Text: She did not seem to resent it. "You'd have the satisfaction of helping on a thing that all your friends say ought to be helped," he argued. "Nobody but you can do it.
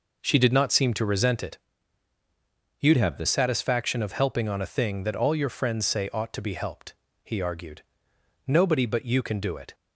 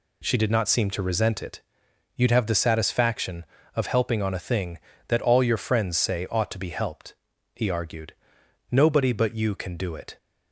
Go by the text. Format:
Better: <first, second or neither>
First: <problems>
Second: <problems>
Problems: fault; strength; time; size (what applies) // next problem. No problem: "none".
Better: second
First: changes voice from "have" to "the"; from 2.9 to 3.2 s; 0.3 s long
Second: none